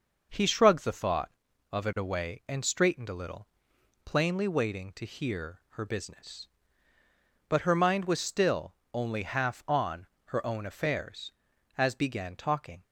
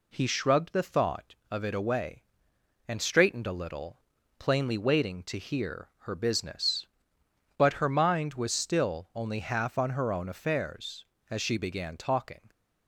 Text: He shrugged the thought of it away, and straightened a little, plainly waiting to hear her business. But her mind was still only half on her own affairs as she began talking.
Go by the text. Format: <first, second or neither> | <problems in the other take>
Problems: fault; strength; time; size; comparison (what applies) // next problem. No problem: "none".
second | pauses between "still" and "only"; slight; at 8.7 s; 0.22 s long // pauses between "on" and "her"; slight; at 10.0 s; 0.20 s long // skips "she"; at 11.9 s